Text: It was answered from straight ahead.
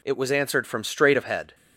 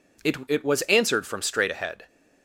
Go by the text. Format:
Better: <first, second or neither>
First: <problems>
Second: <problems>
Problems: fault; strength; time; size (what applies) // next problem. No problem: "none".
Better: first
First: none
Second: says "It" twice; at 0.4 s